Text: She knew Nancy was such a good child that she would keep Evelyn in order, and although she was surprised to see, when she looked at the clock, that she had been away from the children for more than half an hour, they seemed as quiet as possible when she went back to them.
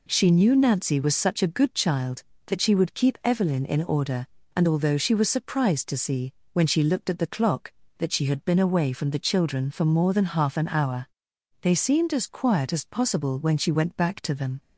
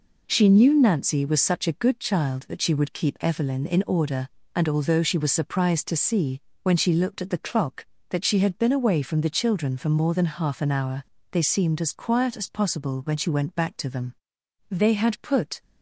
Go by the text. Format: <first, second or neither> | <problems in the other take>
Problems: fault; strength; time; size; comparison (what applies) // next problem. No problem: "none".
first | goes on to say "They had put"; noticeable; from 14.7 s on; 0.90 s long